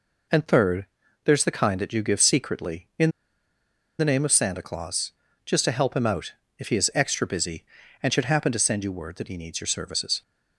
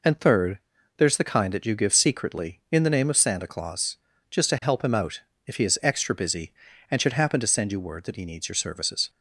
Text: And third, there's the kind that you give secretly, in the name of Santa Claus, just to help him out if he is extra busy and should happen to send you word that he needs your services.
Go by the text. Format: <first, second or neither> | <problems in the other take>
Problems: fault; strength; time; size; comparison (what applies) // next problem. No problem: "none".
second | pauses between "in" and "the"; noticeable; at 3.1 s; 0.88 s long // pauses between "out" and "if"; slight; at 6.3 s; 0.24 s long; slight in the second